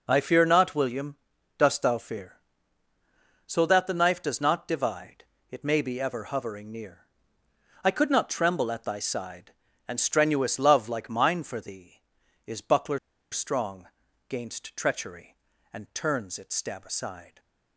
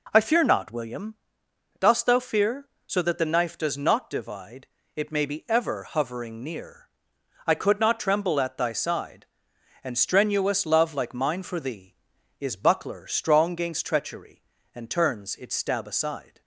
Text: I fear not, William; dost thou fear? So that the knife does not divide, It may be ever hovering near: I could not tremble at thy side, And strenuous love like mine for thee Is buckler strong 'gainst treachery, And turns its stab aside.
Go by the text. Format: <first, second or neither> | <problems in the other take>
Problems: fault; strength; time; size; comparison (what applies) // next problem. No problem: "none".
second | pauses between "buckler" and "strong"; slight; at 12.9 s; 0.33 s long // pauses between "strong" and "gainst"; at 13.8 s; 0.40 s long